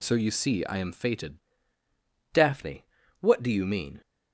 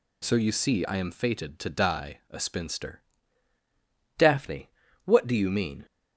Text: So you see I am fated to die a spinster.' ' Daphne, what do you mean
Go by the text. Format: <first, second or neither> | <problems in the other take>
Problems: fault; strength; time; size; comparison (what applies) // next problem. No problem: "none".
second | skips "to die a spinster"; at 1.5 s